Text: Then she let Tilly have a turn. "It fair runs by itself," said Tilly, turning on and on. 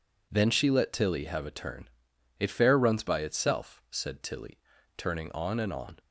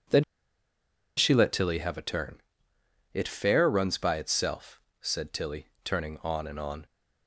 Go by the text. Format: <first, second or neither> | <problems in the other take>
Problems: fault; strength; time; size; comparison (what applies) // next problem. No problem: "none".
first | pauses between "Then" and "she"; noticeable; at 0.2 s; 0.93 s long